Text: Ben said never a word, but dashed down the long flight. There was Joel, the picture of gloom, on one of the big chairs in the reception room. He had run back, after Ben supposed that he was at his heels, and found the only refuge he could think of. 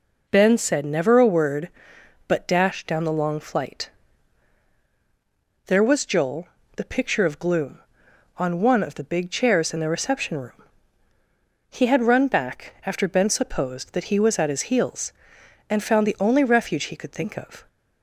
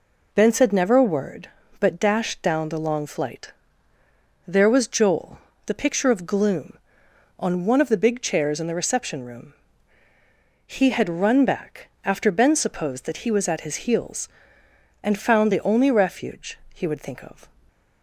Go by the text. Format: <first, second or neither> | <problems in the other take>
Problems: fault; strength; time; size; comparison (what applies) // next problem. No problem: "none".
first | says "would" for "could"; at 16.8 s